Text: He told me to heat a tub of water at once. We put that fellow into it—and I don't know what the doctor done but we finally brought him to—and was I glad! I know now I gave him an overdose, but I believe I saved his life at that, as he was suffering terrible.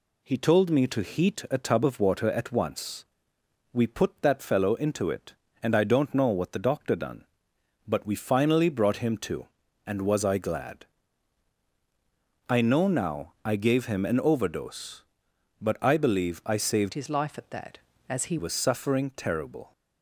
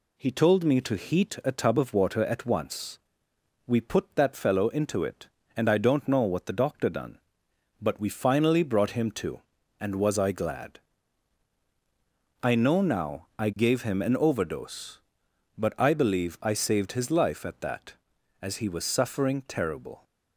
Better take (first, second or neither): second